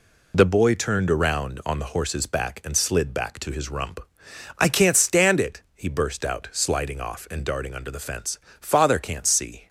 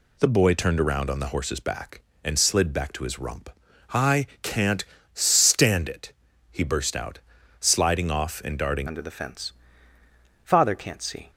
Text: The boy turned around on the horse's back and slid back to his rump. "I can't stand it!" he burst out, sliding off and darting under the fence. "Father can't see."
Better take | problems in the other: first | pauses between "I" and "can't"; slight; at 4.2 s; 0.16 s long // pauses between "can't" and "stand"; slight; at 4.8 s; 0.30 s long // changes voice at "under"; from 8.8 s on; 2.4 s long

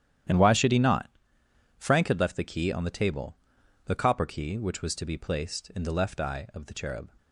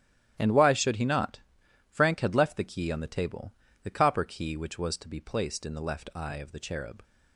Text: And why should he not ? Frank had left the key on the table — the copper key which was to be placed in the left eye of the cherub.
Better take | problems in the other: neither | starts louder than the rest; strong; the same in both

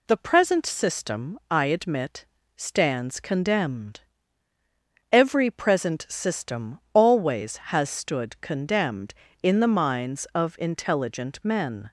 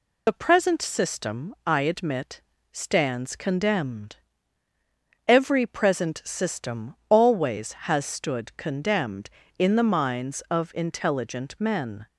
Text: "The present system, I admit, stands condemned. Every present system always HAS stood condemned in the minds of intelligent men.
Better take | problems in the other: first | loses the start of "The"; at 0.2 s; 45 ms

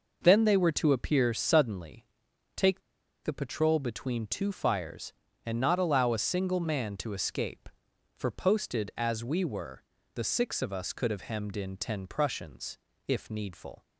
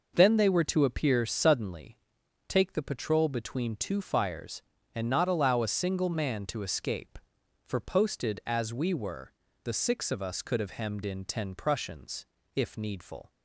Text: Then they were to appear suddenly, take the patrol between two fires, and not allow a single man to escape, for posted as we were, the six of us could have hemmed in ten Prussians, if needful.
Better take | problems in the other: second | pauses between "take" and "the"; at 2.8 s; 0.44 s long

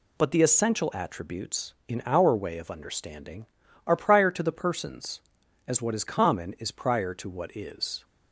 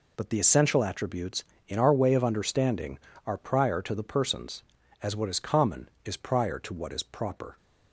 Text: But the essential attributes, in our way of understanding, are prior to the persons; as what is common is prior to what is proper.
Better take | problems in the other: second | stops before "proper"; at 8.0 s

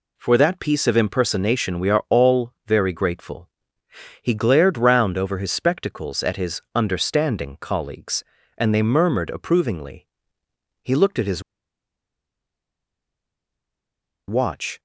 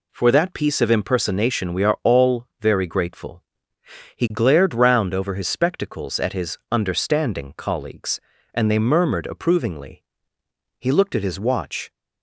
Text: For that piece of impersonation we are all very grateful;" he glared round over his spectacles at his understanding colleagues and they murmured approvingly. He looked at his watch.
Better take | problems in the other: second | pauses between "his" and "watch"; strong; at 11.4 s; 2.8 s long

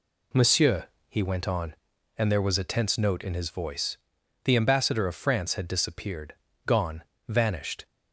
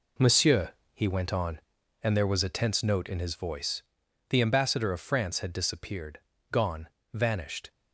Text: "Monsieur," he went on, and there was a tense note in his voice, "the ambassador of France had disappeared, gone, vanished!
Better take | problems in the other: first | gets quieter; strong; throughout; 9.5 dB

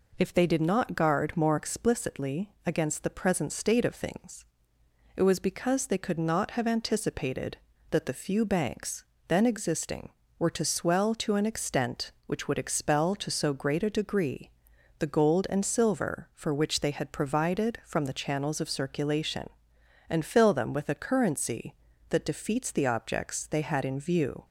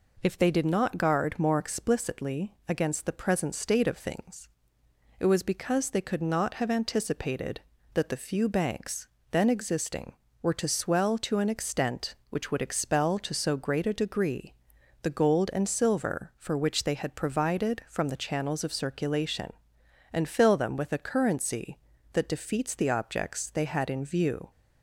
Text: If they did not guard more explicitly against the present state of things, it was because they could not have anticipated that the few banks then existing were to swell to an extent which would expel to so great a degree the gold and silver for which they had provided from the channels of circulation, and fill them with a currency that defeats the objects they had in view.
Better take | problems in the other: neither | pauses between "banks" and "then"; slight; the same in both // pauses between "degree" and "the"; noticeable; the same in both

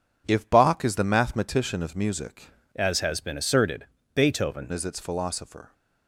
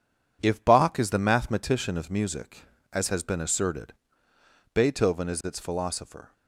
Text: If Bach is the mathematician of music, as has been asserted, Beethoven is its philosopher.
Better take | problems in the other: second | changes voice from "as" to "Beethoven"; from 2.7 to 4.7 s; 2.0 s long

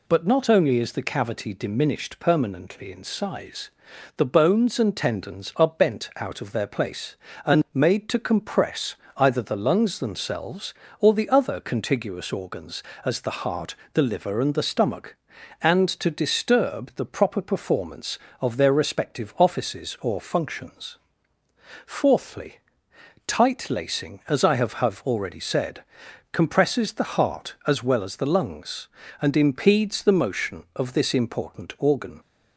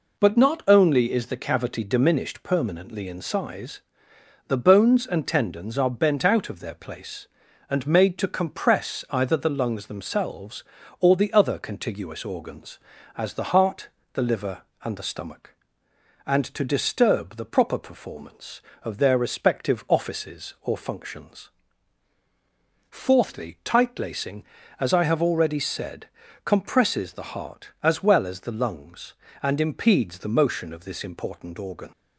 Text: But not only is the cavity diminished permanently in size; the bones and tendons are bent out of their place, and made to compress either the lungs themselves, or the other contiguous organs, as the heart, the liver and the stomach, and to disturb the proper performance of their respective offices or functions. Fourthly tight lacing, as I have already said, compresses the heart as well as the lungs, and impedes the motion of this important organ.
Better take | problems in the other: second | pauses between "compress" and "either"; slight; at 8.9 s; 0.22 s long // pauses between "Fourthly" and "tight"; noticeable; at 22.5 s; 0.68 s long // says "have" twice; at 24.7 s

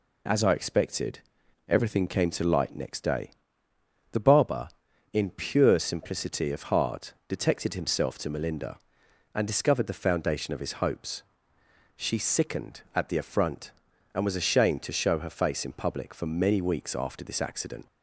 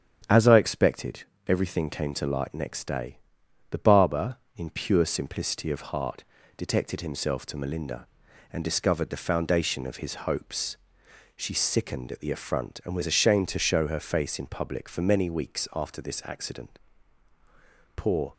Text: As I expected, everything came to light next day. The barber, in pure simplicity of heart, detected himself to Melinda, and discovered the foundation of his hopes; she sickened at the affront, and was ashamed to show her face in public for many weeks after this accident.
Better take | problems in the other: first | starts louder than the rest; strong; until 1.5 s; 8.5 dB // goes on to say "Poor"; slight; from 17.9 s on; 0.36 s long

